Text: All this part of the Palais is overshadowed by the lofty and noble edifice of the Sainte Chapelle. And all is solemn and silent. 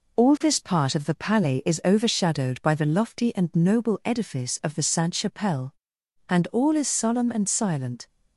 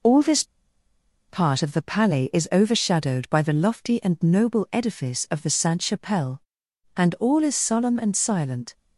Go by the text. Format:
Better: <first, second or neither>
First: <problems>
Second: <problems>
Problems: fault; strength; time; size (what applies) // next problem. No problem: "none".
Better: first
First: none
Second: pauses between "this" and "part"; noticeable; at 0.4 s; 0.85 s long